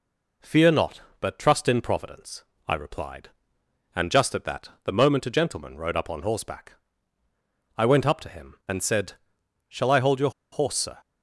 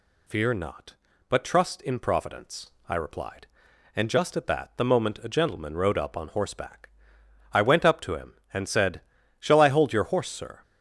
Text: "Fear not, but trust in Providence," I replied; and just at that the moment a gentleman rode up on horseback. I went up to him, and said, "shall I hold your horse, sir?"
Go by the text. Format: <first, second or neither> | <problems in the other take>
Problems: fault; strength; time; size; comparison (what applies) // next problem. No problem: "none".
second | pauses between "your" and "horse"; slight; at 10.2 s; 0.22 s long